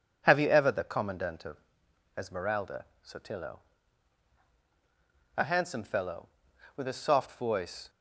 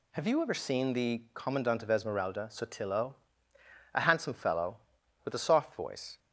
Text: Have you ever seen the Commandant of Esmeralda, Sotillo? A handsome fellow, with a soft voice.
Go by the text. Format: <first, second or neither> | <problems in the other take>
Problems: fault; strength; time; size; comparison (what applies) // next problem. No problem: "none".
second | skips "seen"; at 0.6 s // pauses between "of" and "Esmeralda"; noticeable; at 1.5 s; 0.58 s long